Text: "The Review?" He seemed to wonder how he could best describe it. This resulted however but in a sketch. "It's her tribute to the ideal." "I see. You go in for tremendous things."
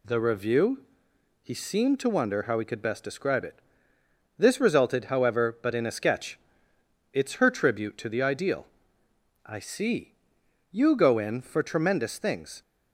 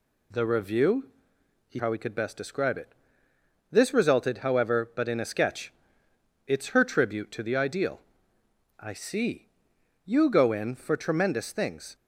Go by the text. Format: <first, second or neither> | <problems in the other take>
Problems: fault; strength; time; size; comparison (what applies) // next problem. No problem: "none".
first | skips "seemed to wonder"; at 1.7 s